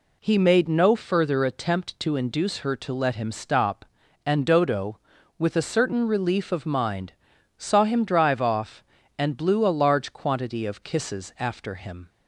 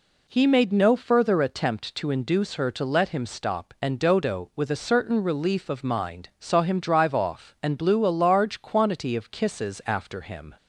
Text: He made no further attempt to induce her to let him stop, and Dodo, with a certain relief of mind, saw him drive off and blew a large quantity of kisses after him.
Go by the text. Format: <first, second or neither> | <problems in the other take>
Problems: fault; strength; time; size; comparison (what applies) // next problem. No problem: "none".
neither | none